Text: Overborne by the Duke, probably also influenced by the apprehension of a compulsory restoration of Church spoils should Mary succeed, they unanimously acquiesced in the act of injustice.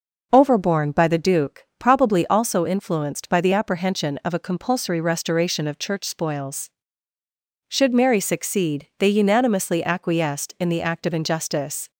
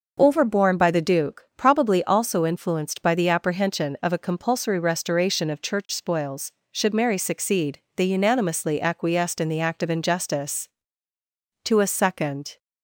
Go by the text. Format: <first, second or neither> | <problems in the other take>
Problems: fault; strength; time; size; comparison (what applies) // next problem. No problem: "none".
first | goes on to say "To a second"; noticeable; from 11.6 s on; 0.94 s long